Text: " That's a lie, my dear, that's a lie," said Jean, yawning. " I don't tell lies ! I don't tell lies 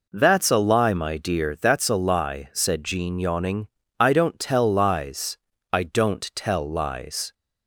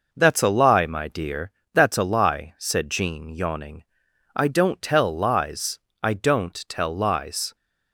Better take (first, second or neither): neither